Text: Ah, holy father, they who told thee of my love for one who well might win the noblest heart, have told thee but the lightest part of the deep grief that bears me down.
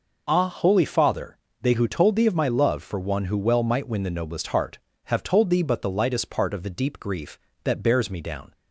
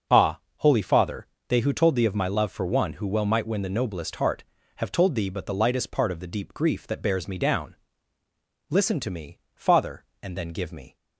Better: first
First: none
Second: starts louder than the rest; until 1.5 s; 6 dB // goes on to say "Listen to me Father and then give me"; strong; from 8.6 s on; 2.2 s long

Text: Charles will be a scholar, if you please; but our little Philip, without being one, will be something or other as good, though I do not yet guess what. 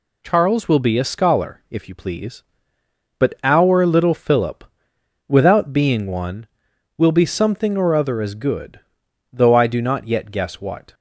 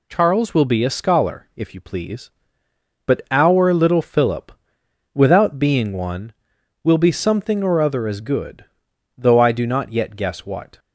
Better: neither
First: none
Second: none

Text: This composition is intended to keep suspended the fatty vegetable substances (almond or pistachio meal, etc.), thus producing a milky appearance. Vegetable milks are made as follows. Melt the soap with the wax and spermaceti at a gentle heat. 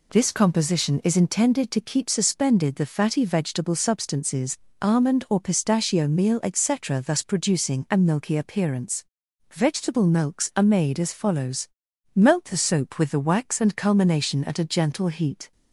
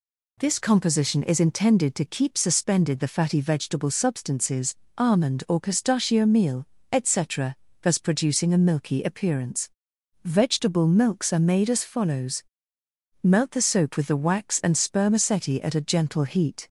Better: second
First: says "culmination" for "spermaceti"; at 13.7 s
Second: none

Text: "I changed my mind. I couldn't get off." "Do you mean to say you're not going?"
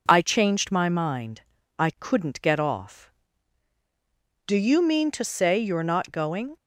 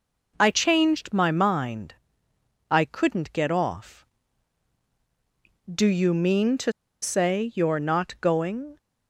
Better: first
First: none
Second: pauses between "to" and "say"; slight; at 6.7 s; 0.30 s long

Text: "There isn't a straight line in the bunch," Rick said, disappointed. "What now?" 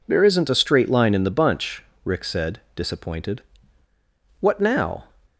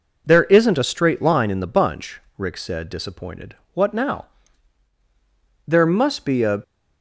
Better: first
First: none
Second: goes on to say "There must be a"; noticeable; from 5.6 s on; 0.96 s long

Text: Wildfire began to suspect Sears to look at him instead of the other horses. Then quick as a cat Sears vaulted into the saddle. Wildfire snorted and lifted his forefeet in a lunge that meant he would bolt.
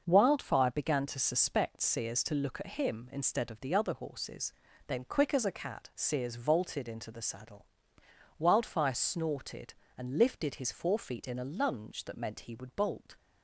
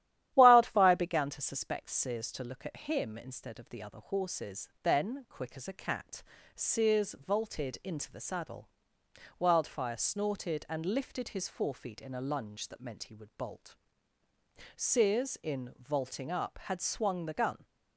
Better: first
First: starts louder than the rest; noticeable; until 1.0 s; 6 dB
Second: starts louder than the rest; strong; until 1.3 s; 12 dB // pauses between "cat" and "Sears"; slight; at 6.2 s; 0.32 s long // goes on to say "Sears in vaulting up had swung the gun"; strong; from 14.7 s on; 2.9 s long

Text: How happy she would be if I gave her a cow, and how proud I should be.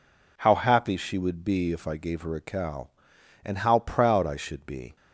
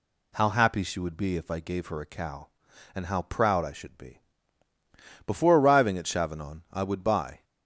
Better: first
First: none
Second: goes on to say "Before arriving at Chavanon I would buy"; strong; from 5.2 s on; 2.1 s long

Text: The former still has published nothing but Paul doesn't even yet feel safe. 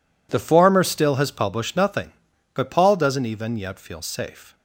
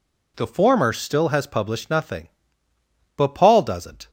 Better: first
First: none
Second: stops before "even yet feel safe"; at 4.0 s

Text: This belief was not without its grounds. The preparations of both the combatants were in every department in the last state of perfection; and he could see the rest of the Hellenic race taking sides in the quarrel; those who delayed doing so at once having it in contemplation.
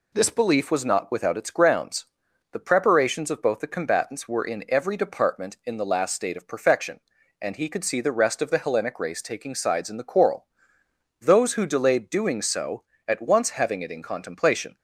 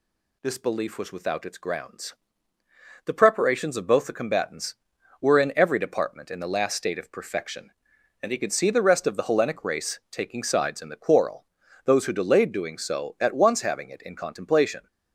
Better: first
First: none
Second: skips "not"; at 1.1 s

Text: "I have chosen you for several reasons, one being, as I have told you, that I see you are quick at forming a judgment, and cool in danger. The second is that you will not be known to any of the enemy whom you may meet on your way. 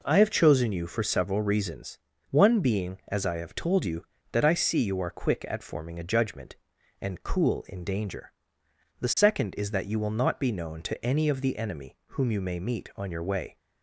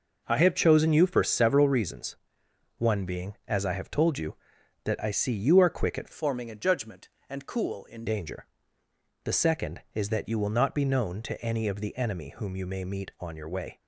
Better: first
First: none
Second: changes voice from "forming" to "in"; from 6.1 to 8.0 s; 1.9 s long

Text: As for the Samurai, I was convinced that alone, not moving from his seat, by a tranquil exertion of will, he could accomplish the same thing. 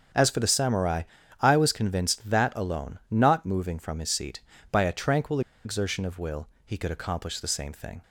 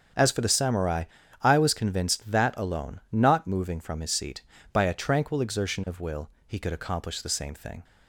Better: second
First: starts louder than the rest; strong; until 1.5 s; 7.5 dB // pauses between "tranquil" and "exertion"; slight; at 5.4 s; 0.24 s long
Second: starts louder than the rest; strong; until 1.5 s; 8 dB

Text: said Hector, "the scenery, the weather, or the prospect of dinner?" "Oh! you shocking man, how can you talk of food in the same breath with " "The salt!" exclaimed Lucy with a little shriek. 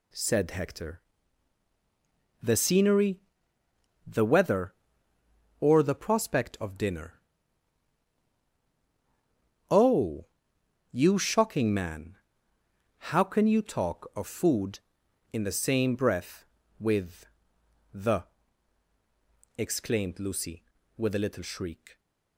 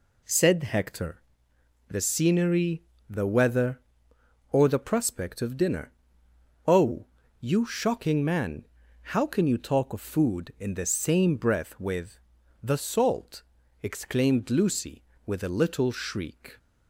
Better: second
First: skips "salt"; at 18.9 s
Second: none

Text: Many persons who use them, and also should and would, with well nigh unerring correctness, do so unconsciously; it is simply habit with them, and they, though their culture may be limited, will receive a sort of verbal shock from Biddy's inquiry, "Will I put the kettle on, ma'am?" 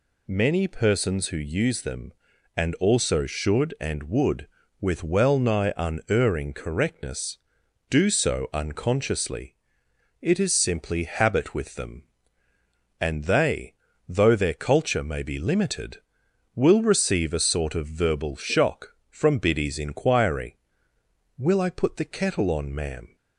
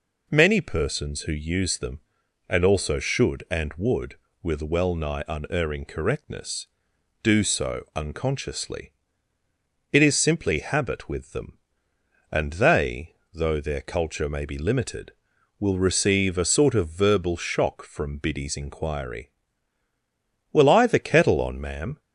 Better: first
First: none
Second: skips "put"; at 20.8 s

